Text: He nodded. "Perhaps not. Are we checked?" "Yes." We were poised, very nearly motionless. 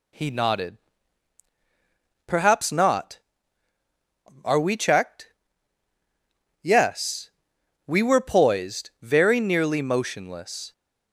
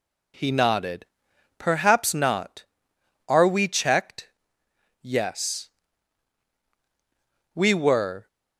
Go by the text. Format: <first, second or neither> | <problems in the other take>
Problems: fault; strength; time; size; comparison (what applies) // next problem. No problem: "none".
first | stops before "poised very nearly motionless"; at 8.2 s